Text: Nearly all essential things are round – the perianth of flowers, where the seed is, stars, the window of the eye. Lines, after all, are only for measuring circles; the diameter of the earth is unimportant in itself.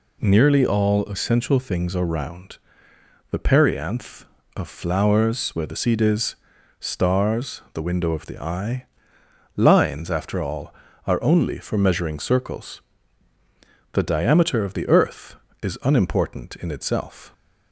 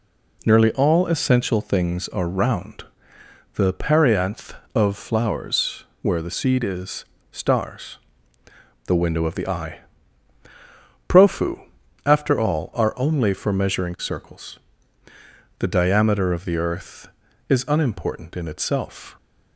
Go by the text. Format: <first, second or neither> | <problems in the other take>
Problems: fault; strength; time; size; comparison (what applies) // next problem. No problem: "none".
first | says "Profu" for "Lines"; at 11.0 s